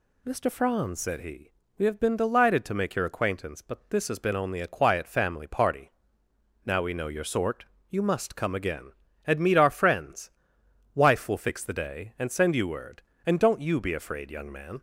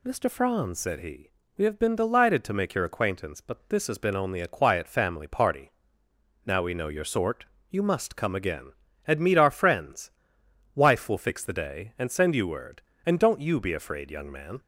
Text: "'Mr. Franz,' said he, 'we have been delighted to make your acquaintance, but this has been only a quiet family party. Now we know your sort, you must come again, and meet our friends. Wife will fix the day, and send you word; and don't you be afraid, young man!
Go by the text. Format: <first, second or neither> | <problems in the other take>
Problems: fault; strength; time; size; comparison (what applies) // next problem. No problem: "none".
neither | none